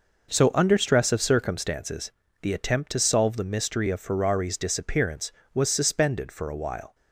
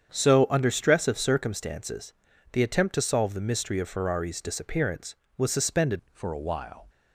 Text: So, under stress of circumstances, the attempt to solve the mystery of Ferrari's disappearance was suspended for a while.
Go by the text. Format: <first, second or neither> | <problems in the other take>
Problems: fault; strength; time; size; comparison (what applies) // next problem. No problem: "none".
first | starts louder than the rest; strong; until 1.1 s; 8 dB // changes voice at "for"; from 6.1 s on; 0.7 s long